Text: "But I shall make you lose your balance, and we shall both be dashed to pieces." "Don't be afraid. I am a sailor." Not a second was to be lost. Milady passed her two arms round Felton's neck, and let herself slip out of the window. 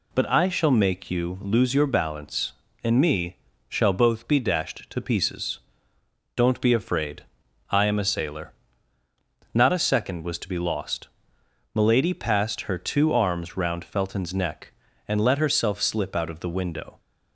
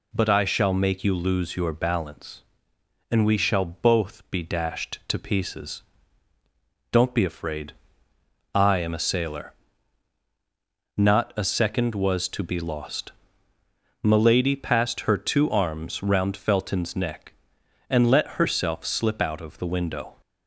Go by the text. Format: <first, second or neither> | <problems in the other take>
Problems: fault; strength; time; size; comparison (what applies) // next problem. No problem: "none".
second | says "me" for "we"; at 2.9 s